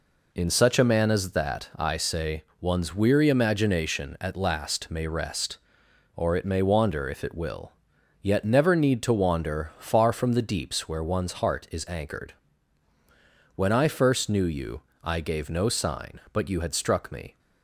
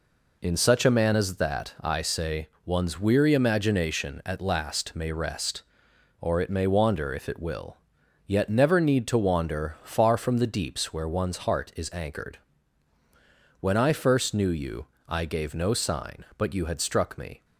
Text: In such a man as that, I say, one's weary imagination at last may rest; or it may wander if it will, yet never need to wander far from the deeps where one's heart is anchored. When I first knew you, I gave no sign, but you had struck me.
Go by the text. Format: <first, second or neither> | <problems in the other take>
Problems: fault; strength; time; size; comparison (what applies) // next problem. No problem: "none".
neither | none